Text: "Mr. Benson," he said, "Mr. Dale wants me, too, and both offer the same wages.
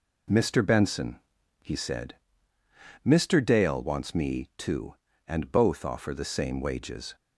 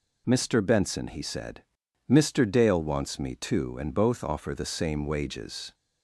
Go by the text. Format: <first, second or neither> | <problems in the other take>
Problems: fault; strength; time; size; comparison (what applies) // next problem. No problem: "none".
neither | none